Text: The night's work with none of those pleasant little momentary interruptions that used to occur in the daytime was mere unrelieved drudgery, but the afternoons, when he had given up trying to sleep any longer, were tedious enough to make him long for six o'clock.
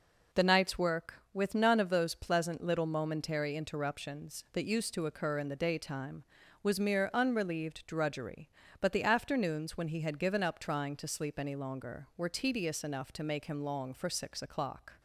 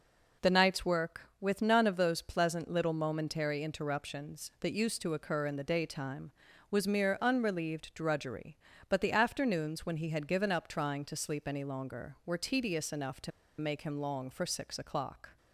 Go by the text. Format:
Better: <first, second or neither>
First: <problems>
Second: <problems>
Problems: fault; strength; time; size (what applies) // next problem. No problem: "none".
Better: first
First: none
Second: pauses between "to" and "make"; slight; at 13.3 s; 0.30 s long